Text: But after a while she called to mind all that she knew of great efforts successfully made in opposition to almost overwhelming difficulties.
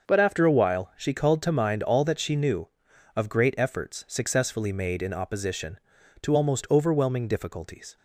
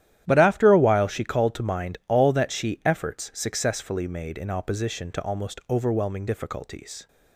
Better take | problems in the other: first | starts louder than the rest; strong; until 1.2 s; 12 dB; also in the first // skips "knew of great"; at 2.8 s

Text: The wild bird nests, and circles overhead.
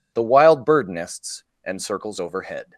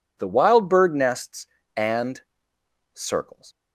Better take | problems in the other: first | pauses between "and" and "circles"; noticeable; at 2.2 s; 0.72 s long // stops before "overhead"; at 3.5 s

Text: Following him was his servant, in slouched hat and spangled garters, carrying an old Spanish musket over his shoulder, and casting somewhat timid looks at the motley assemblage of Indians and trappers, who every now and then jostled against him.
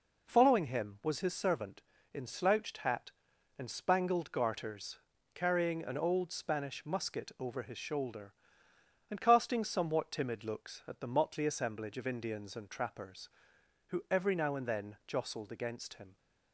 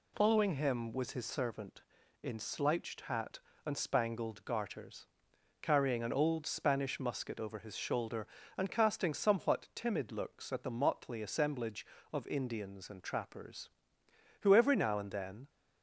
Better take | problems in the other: first | stops before "jostled against him"; at 15.4 s

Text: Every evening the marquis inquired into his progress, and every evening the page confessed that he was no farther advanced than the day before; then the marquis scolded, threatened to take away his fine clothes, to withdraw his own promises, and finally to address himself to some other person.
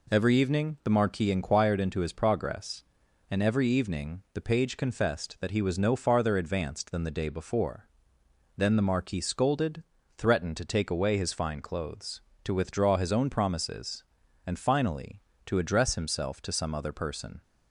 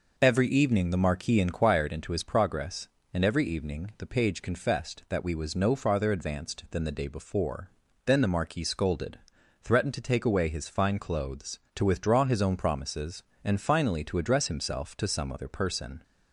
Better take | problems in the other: first | says "we" for "he"; at 5.2 s

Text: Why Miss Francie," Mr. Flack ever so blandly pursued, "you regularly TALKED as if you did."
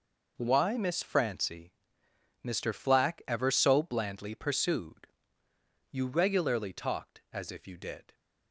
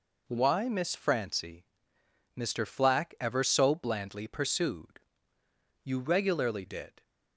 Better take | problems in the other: first | skips "TALKED as if you"; at 6.6 s

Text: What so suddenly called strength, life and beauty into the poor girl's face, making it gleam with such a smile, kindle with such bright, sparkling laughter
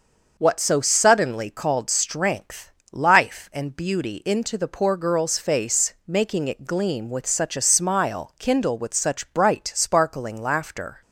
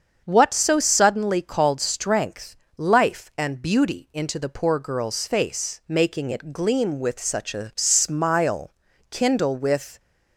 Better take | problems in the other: first | starts louder than the rest; strong; until 1.2 s; 7 dB; noticeable in the first // stops before "such bright sparkling laughter"; at 9.9 s

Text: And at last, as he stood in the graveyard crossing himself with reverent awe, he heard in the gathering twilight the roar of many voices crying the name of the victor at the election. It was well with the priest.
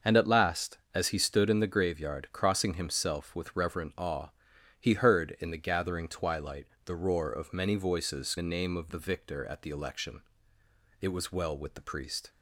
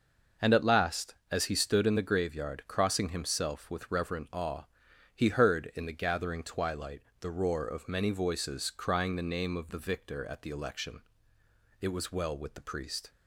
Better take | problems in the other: second | starts louder than the rest; until 1.2 s; 6 dB // pauses between "twilight" and "the"; slight; at 6.6 s; 0.20 s long; slight in the second // skips "crying"; at 8.3 s

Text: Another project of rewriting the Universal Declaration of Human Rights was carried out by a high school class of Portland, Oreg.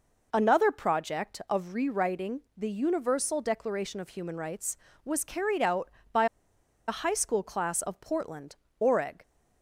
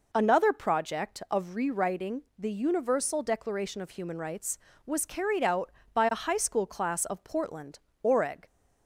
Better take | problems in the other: second | pauses between "by" and "a"; noticeable; at 6.2 s; 0.61 s long

